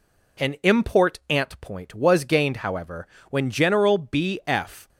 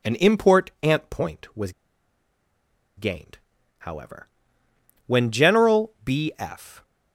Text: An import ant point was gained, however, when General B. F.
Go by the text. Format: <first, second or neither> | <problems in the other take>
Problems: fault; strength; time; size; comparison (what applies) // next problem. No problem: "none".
first | pauses between "was" and "gained"; strong; at 1.7 s; 1.2 s long